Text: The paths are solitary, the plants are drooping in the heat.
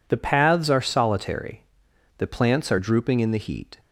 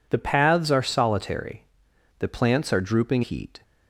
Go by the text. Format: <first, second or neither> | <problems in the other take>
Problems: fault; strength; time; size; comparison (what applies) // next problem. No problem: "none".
first | skips "in the"; at 3.2 s